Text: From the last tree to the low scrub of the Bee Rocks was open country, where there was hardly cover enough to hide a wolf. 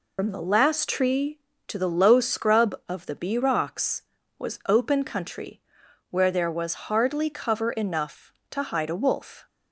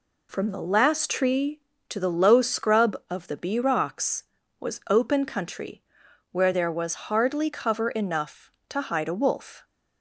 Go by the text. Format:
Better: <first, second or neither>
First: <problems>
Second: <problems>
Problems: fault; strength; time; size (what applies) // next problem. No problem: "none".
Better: second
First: loses the start of "From"; at 0.1 s; 75 ms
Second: none